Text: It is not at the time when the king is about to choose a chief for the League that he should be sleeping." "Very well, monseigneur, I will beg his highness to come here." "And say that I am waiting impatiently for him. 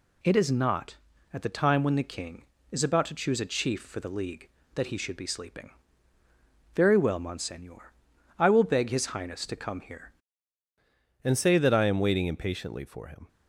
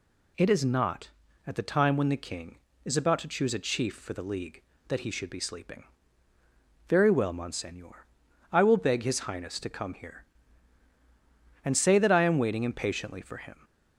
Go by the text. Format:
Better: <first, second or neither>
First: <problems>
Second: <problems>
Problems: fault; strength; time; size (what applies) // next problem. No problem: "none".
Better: second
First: changes voice at "And"; from 11.2 s on; 2.0 s long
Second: none